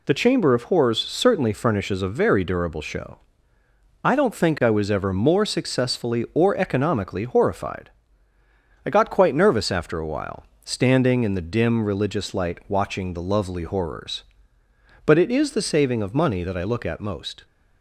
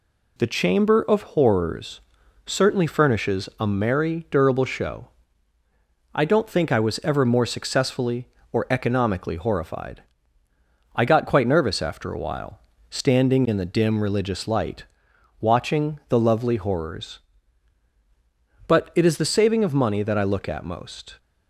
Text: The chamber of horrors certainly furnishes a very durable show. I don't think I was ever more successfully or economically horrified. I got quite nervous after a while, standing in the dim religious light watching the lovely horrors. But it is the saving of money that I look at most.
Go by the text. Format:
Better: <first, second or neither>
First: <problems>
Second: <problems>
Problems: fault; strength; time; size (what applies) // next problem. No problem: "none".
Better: first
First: none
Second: pauses between "horrors" and "certainly"; at 2.0 s; 0.44 s long // says "merry" for "very"; at 3.6 s // pauses between "light" and "watching"; noticeable; at 14.8 s; 0.56 s long